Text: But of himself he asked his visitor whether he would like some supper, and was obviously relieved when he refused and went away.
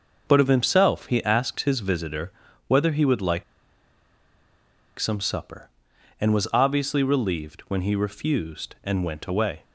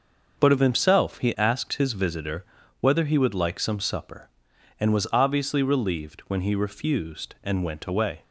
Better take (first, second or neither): second